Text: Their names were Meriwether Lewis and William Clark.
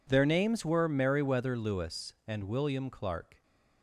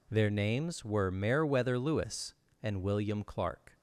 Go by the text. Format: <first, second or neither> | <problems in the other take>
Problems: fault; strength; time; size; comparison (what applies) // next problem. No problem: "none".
neither | none